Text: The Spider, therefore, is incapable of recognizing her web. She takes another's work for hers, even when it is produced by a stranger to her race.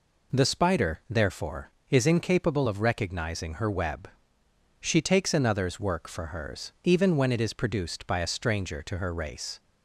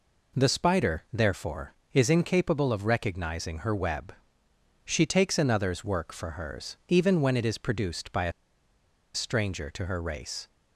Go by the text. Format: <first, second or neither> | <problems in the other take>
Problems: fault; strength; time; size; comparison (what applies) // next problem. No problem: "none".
first | pauses between "a" and "stranger"; noticeable; at 8.3 s; 0.82 s long